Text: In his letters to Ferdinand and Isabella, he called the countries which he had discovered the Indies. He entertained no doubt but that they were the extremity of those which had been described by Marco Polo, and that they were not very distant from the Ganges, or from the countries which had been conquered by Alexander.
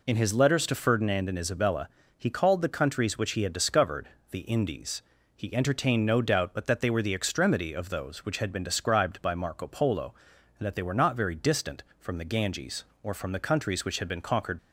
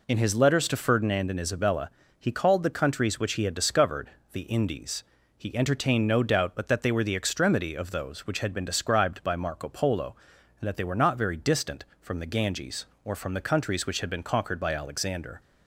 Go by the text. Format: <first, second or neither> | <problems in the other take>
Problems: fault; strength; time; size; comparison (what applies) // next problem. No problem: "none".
second | pauses between "discovered" and "the"; slight; at 4.0 s; 0.22 s long; slight in the second // stops before "by Alexander"; at 14.5 s